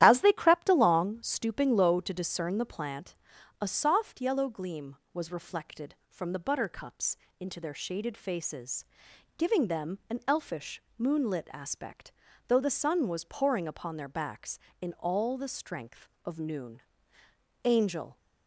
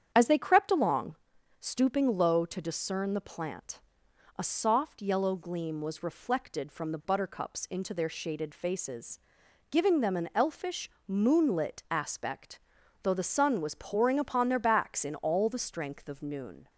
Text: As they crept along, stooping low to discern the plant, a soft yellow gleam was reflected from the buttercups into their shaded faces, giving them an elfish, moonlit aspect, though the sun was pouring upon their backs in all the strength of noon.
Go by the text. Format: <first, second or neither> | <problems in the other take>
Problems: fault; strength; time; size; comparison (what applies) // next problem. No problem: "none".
second | starts louder than the rest; strong; until 1.0 s; 11.5 dB; strong in the second // pauses between "buttercups" and "into"; slight; at 7.1 s; 0.22 s long // goes on to say "Angel"; from 17.6 s on; 0.54 s long